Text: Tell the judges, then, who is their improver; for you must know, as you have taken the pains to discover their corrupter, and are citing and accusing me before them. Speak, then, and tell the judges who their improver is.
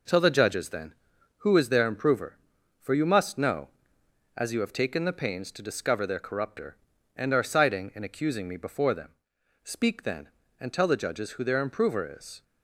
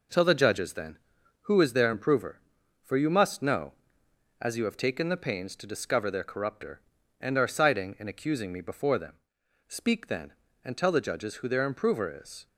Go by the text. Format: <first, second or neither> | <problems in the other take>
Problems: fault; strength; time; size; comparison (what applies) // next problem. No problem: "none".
neither | none